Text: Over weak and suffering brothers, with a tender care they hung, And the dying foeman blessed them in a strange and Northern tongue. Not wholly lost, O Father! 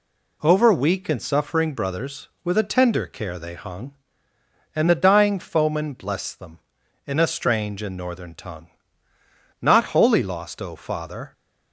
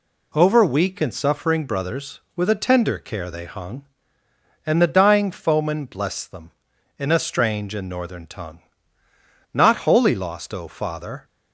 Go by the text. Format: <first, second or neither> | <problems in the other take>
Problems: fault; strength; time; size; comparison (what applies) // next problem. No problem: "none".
neither | none